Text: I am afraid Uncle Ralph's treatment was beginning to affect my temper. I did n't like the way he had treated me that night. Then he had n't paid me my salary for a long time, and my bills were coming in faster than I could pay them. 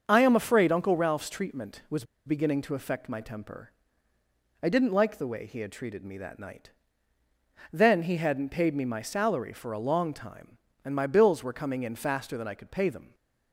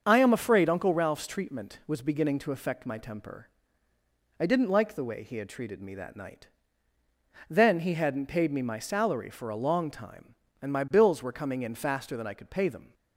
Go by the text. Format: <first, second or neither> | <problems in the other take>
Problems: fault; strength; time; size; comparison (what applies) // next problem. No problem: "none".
second | starts louder than the rest; until 1.0 s; 6.5 dB; also in the second // pauses between "was" and "beginning"; slight; at 2.0 s; 0.22 s long